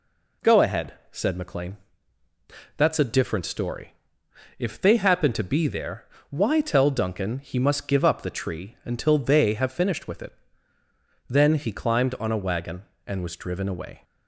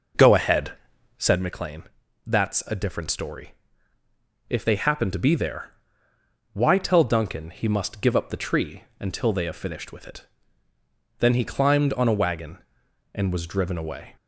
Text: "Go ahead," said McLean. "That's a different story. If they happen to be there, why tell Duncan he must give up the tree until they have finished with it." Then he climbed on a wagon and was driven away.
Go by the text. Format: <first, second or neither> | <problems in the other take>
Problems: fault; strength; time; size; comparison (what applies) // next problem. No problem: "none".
first | starts louder than the rest; noticeable; until 1.5 s; 5.5 dB